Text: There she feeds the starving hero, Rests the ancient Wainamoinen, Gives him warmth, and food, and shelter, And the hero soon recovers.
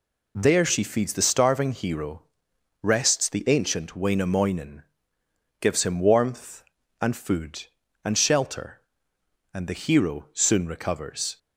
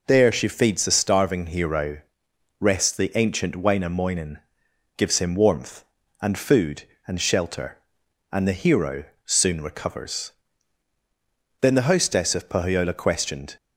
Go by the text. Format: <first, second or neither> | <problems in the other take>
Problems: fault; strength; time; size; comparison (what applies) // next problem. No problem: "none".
first | pauses between "hero" and "soon"; slight; at 9.0 s; 0.20 s long // goes on to say "Then the hostess of Pohyola Questioned"; strong; from 11.6 s on; 1.9 s long